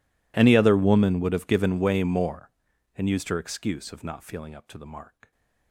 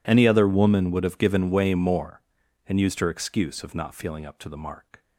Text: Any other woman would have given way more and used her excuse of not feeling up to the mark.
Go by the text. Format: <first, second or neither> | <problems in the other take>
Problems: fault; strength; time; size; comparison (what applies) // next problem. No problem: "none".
second | gets quieter; strong; throughout; 30 dB